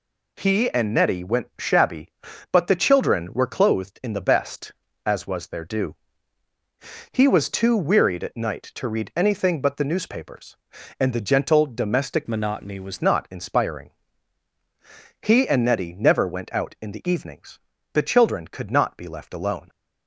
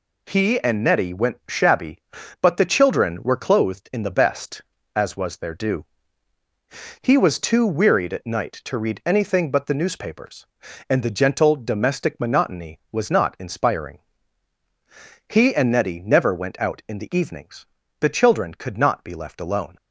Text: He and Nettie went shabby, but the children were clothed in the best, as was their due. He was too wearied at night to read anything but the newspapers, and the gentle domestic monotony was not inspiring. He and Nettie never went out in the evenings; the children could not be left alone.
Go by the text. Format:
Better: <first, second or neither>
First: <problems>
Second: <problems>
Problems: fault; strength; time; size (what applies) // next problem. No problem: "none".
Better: second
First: changes voice from "monotony" to "was"; from 12.2 to 13.0 s; 0.8 s long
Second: none